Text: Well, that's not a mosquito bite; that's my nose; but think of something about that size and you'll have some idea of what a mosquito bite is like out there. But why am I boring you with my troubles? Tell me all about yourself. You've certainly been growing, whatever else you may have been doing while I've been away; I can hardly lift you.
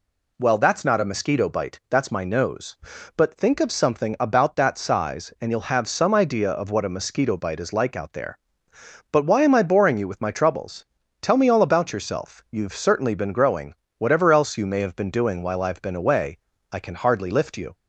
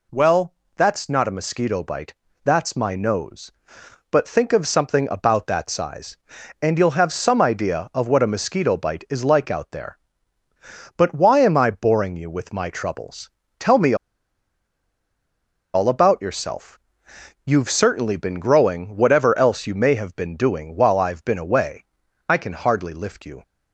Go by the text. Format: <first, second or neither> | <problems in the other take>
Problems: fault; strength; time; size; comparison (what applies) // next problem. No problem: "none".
first | pauses between "me" and "all"; strong; at 13.9 s; 1.7 s long